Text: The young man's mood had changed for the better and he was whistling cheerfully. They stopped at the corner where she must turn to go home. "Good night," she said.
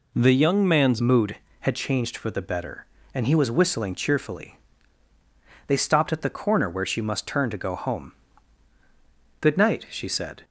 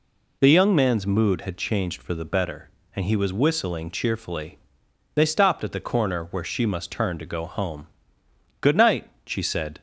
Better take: second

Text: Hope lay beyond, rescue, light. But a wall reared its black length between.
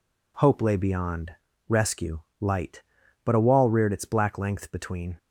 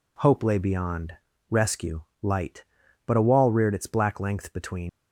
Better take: first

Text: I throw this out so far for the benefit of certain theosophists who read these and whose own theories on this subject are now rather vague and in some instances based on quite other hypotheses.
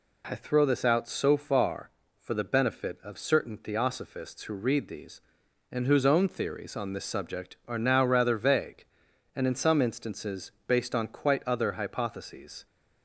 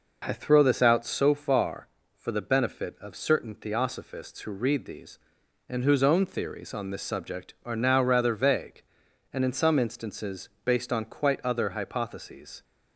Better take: first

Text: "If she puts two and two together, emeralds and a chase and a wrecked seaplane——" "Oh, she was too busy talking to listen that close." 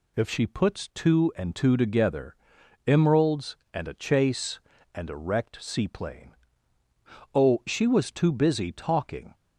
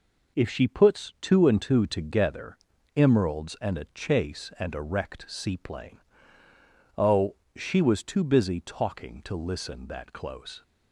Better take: second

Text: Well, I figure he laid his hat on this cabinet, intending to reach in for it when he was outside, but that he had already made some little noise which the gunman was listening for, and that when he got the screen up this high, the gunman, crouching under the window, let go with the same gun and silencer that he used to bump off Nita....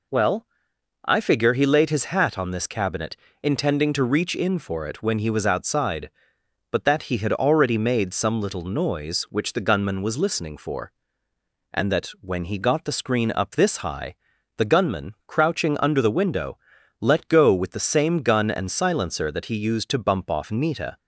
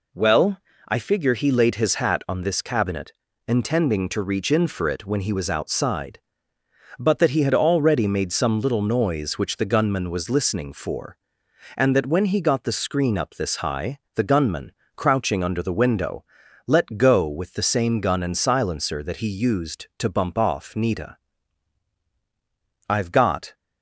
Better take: first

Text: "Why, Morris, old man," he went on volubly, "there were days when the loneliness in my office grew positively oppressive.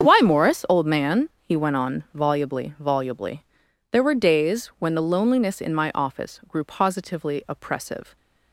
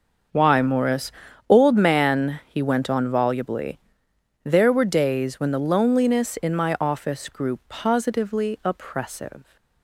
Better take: second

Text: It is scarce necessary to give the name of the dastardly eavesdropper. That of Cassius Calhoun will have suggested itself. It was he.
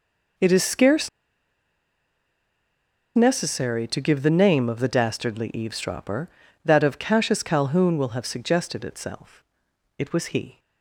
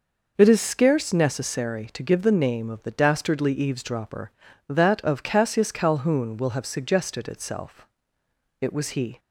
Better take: second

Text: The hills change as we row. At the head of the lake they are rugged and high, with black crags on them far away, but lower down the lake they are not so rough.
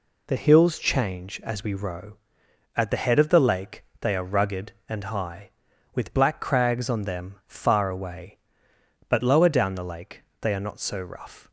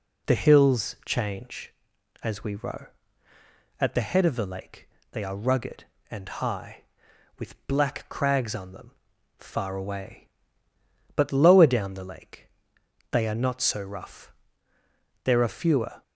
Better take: first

